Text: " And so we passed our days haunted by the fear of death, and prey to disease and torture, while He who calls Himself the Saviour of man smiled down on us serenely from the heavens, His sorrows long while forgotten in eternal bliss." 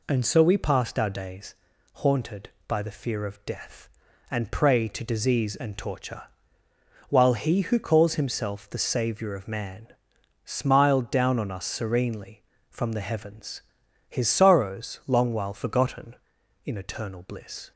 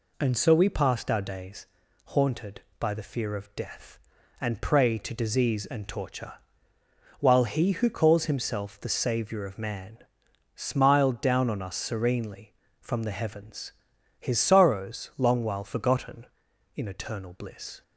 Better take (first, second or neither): neither